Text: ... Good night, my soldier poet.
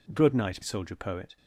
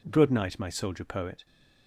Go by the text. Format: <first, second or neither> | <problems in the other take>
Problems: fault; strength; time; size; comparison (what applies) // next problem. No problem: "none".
second | skips "my"; at 0.6 s